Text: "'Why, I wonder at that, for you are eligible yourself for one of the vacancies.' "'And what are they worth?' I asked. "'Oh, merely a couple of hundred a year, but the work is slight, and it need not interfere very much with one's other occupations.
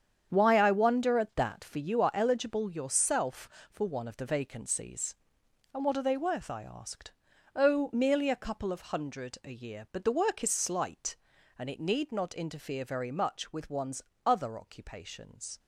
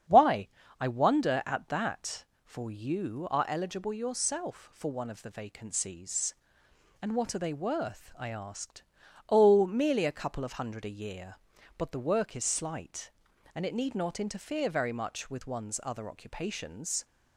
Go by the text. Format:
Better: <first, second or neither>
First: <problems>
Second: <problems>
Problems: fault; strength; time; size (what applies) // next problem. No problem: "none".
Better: second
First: gets quieter; strong; throughout; 10.5 dB // starts louder than the rest; strong; until 1.3 s; 8 dB // pauses between "one's" and "other"; slight; at 14.0 s; 0.24 s long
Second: starts louder than the rest; strong; until 1.4 s; 8 dB